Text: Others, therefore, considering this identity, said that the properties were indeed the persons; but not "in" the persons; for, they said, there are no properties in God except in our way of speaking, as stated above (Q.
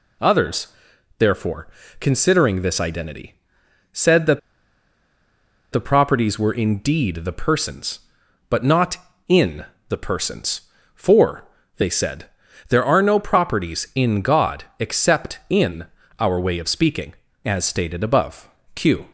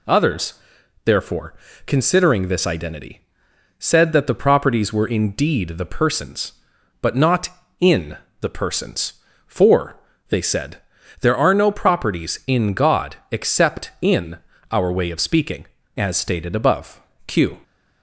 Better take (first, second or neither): second